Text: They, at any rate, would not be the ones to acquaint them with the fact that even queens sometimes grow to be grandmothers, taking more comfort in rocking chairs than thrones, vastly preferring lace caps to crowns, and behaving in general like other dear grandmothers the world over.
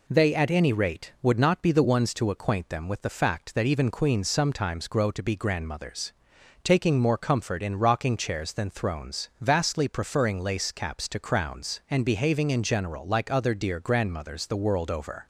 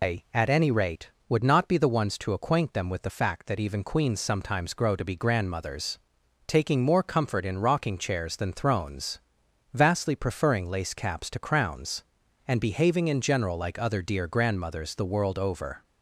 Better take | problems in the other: first | loses the start of "They"; at 0.0 s; 160 ms

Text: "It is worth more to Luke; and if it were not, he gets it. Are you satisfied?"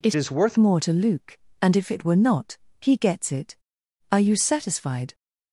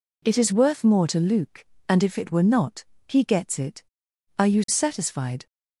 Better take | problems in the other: second | changes voice from "is" to "worth"; from 0.1 to 0.5 s; 0.4 s long

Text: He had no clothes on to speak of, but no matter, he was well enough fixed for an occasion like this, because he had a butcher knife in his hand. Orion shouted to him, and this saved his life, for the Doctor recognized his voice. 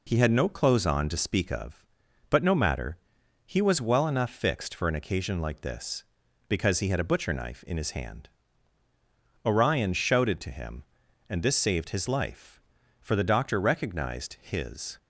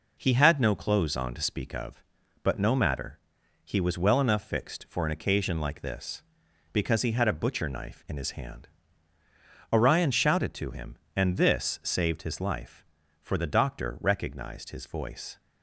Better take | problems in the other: second | stops before "voice"; at 14.9 s

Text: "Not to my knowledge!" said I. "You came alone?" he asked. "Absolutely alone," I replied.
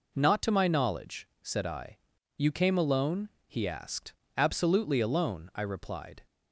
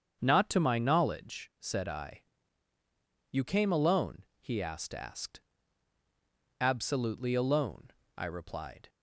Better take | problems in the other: first | starts louder than the rest; strong; until 1.2 s; 7 dB // says "asked" twice; at 4.9 s

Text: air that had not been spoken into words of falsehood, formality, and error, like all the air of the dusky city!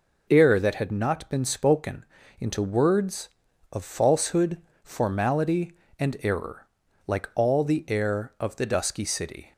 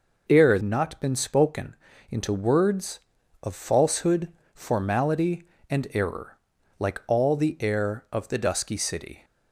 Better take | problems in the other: first | skips "that had"; at 0.6 s // pauses between "spoken" and "into"; slight; at 1.7 s; 0.36 s long; slight in the first

